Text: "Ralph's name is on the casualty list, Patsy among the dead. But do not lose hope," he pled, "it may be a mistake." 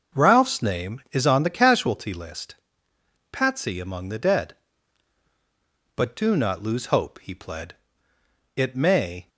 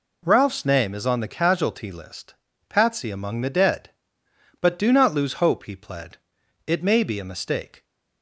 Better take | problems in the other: second | stops before "be a mistake"; at 9.2 s

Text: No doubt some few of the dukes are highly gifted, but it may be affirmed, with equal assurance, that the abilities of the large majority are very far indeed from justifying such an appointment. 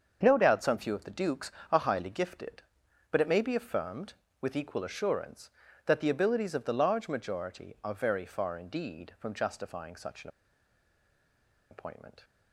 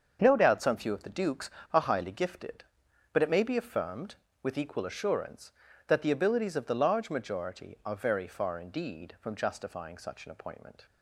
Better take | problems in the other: second | starts louder than the rest; until 1.2 s; 7 dB; also in the second // pauses between "an" and "appointment"; strong; at 10.2 s; 1.4 s long

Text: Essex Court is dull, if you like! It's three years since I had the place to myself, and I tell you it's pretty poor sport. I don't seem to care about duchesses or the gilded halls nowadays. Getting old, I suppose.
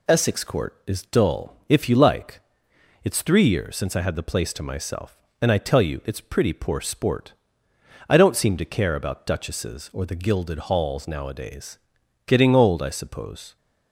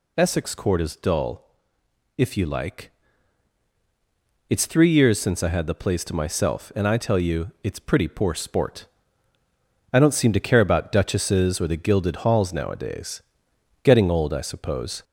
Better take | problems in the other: first | gets louder; throughout; 4 dB

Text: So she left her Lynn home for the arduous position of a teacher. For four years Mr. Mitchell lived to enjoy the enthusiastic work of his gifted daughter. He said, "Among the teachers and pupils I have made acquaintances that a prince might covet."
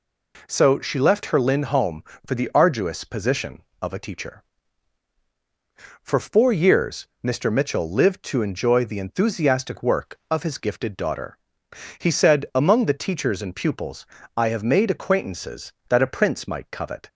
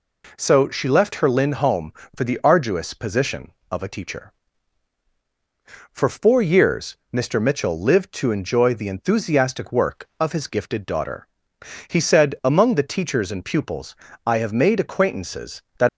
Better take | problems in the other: first | pauses between "pupils" and "I"; slight; at 13.9 s; 0.32 s long; slight in the first // stops before "a prince might covet"; at 15.8 s

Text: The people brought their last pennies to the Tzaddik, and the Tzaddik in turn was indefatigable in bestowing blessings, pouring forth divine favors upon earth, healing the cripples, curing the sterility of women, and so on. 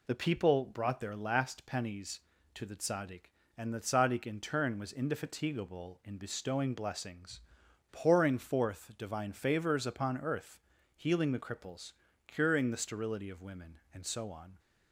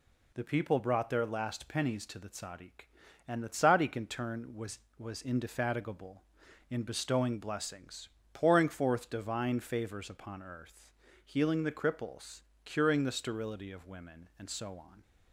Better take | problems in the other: first | says "was" twice; at 4.9 s

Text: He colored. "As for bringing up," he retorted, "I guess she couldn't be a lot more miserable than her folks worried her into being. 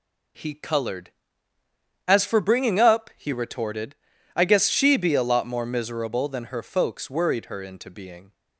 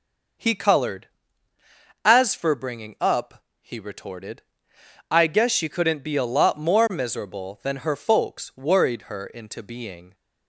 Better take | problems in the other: second | skips "couldn't"; at 4.9 s

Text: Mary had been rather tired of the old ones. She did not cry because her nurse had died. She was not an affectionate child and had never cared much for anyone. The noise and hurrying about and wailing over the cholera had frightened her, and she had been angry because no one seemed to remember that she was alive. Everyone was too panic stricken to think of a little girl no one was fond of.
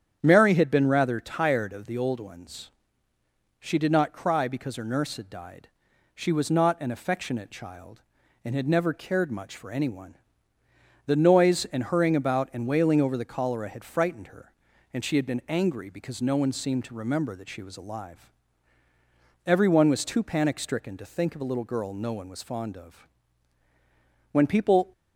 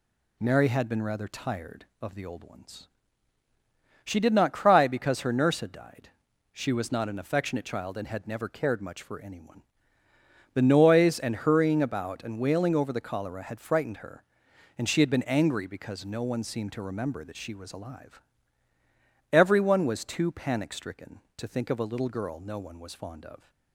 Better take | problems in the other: second | starts louder than the rest; strong; until 1.2 s; 8.5 dB // goes on to say "When people"; from 24.3 s on; 0.60 s long

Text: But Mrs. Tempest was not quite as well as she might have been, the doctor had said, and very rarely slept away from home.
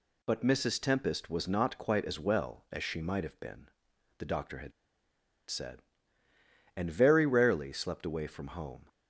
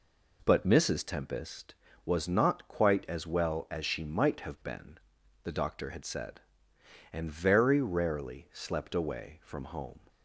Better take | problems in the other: second | pauses between "had" and "said"; noticeable; at 4.7 s; 0.76 s long

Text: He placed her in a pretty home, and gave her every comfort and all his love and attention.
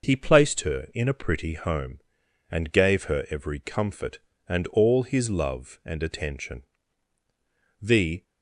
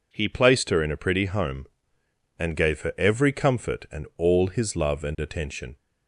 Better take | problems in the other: second | goes on to say "The"; slight; from 7.8 s on; 0.42 s long

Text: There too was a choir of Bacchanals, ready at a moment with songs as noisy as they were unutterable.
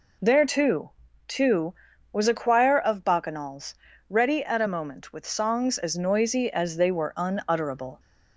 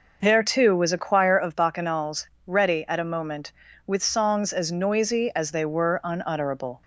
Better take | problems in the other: second | says "too" twice; at 1.2 s

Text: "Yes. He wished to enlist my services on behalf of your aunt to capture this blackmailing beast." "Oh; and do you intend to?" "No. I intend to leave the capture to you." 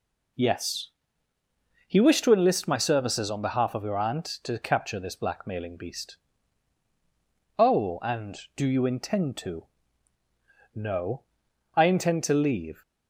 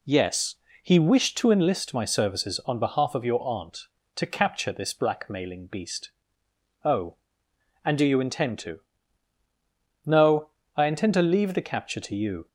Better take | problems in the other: second | stops before "the capture to you"; at 12.8 s

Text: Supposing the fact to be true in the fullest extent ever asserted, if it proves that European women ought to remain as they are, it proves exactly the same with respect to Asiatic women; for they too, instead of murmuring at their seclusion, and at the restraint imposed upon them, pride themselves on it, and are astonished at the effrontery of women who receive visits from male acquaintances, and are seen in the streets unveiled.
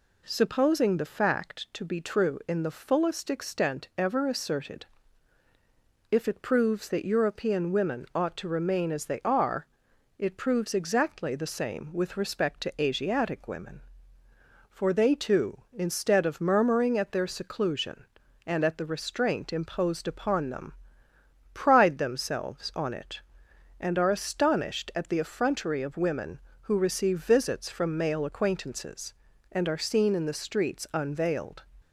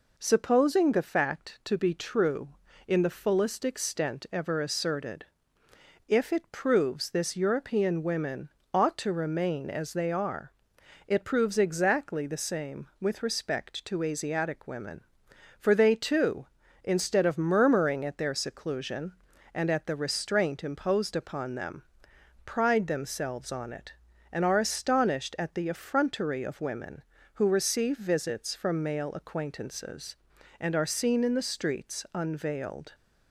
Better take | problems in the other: first | says "this" for "that"; at 7.1 s // pauses between "women" and "ought"; slight; at 8.4 s; 0.24 s long

